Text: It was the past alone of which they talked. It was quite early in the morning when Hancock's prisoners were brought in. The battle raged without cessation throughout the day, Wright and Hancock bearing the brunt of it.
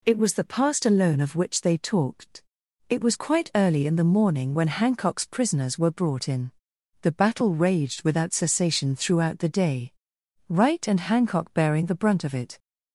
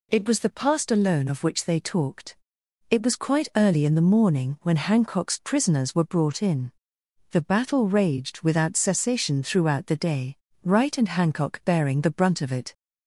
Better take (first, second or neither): neither